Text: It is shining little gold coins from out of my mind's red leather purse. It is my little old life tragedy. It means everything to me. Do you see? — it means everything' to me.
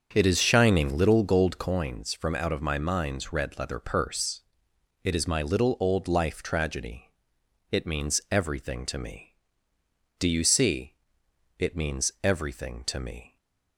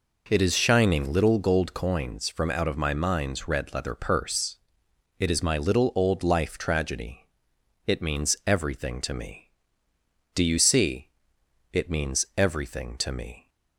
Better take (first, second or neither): second